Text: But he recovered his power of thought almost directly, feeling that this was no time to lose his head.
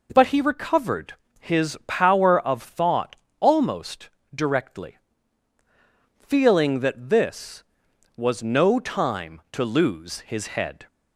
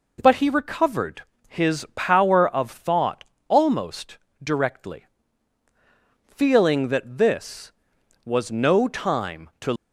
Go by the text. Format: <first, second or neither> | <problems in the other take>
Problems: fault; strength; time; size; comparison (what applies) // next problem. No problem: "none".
first | pauses between "recovered" and "his"; slight; at 1.2 s; 0.24 s long; slight in the first // pauses between "thought" and "almost"; slight; at 3.2 s; 0.24 s long; slight in the first // pauses between "almost" and "directly"; slight; at 4.1 s; 0.26 s long; slight in the first // stops before "lose his head"; at 9.7 s